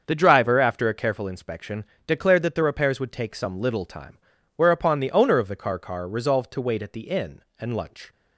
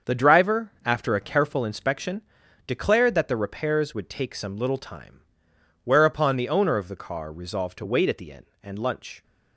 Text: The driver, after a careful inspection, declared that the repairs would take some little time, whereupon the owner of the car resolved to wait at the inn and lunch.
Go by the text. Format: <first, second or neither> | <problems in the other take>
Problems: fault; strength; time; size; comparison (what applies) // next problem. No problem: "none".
second | starts louder than the rest; until 1.0 s; 7 dB; also in the second // says "car" twice; at 5.7 s